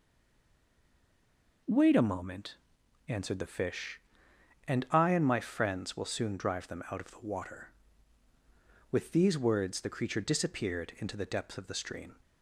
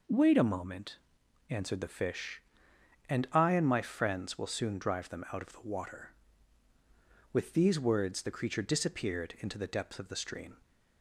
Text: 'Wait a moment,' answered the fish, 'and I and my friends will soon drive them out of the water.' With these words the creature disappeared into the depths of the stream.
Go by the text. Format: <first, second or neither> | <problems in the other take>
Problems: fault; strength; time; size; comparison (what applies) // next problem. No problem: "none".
second | stays silent before the first word; noticeable; until 1.6 s; 1.6 s long